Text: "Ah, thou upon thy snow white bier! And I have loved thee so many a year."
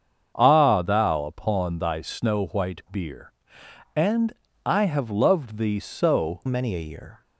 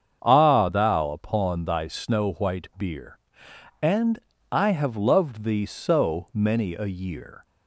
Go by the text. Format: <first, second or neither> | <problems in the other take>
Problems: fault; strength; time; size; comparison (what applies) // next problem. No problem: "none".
second | starts louder than the rest; strong; until 1.3 s; 7 dB; strong in the second // pauses between "And" and "I"; slight; at 4.3 s; 0.34 s long; slight in the second // changes voice at "many"; from 6.4 s on; 0.8 s long